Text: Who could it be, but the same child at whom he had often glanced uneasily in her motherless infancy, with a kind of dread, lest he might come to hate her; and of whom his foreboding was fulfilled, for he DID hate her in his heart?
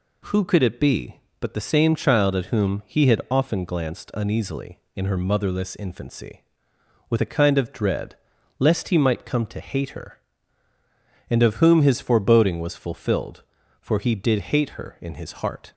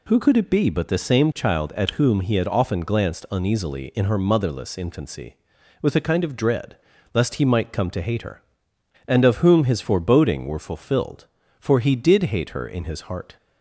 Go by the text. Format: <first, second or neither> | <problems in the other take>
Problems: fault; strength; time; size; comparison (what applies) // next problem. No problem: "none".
first | says "were" for "was"; at 10.4 s